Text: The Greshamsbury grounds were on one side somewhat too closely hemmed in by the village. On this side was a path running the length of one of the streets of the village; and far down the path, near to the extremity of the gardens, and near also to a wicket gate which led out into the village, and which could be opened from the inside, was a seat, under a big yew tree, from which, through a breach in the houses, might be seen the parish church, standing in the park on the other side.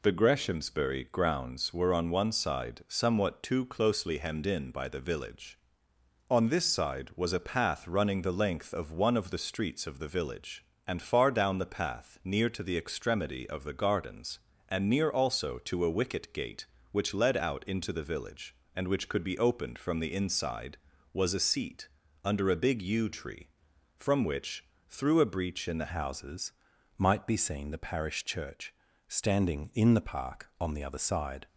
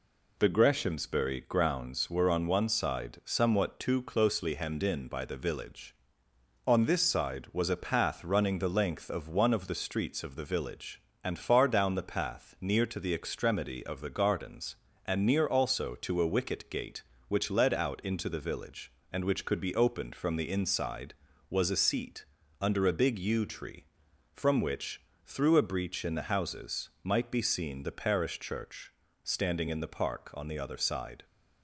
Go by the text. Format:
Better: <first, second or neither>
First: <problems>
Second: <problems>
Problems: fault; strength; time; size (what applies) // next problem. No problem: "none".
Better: second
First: changes voice at "houses"; from 25.8 s on; 5.6 s long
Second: none